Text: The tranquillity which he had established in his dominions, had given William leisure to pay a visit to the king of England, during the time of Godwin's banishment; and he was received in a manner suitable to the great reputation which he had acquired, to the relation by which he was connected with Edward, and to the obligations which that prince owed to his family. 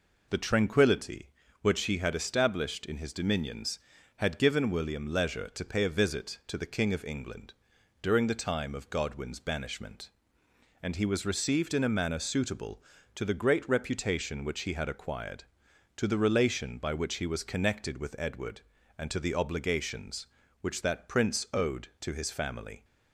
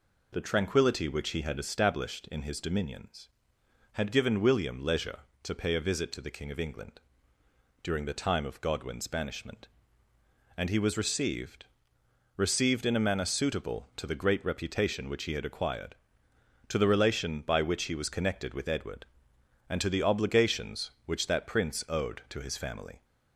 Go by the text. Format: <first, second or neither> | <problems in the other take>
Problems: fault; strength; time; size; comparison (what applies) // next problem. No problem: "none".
first | says "received" twice; at 12.3 s